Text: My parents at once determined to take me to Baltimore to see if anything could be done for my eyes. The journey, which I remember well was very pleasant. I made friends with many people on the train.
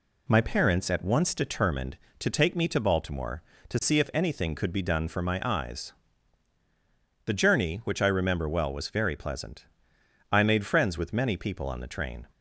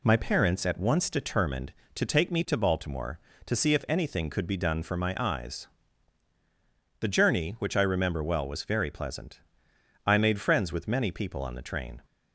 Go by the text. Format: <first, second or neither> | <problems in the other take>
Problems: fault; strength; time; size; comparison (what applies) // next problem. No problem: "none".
neither | none